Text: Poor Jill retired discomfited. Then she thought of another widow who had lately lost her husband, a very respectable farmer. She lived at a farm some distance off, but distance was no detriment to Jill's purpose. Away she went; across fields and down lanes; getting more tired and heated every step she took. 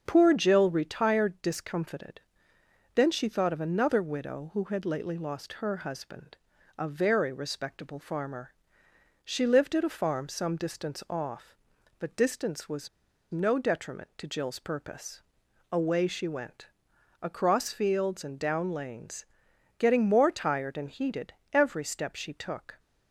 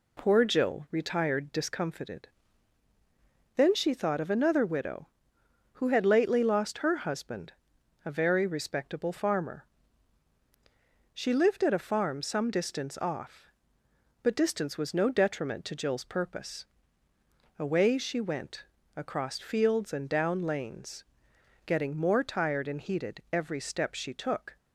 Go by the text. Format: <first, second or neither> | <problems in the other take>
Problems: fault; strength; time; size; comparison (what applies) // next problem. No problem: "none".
second | starts louder than the rest; until 1.0 s; 7 dB // pauses between "was" and "no"; at 12.8 s; 0.42 s long // pauses between "heated" and "every"; slight; at 21.3 s; 0.20 s long